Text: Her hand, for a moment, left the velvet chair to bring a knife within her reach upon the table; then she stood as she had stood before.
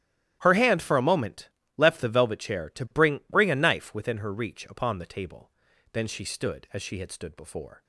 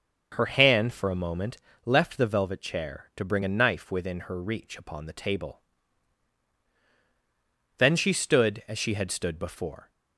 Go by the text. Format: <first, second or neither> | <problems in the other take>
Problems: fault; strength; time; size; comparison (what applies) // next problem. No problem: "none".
second | starts louder than the rest; strong; until 1.4 s; 12.5 dB; also in the second // says "bring" twice; at 3.2 s